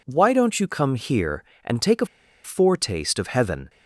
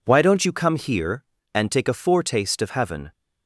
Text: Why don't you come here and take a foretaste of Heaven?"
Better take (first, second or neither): second